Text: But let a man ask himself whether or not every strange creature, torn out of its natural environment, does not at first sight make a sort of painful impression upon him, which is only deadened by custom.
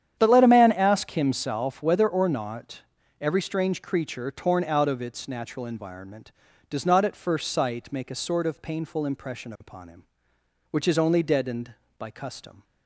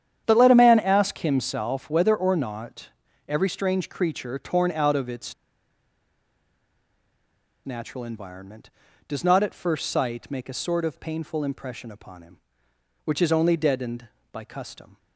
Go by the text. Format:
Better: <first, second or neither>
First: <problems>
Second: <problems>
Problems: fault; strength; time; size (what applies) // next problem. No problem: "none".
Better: first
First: starts louder than the rest; strong; until 1.1 s; 9.5 dB // pauses between "not" and "every"; at 2.8 s; 0.40 s long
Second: starts louder than the rest; strong; until 1.2 s; 9.5 dB // pauses between "not" and "every"; at 2.8 s; 0.40 s long // pauses between "its" and "natural"; strong; at 5.3 s; 2.3 s long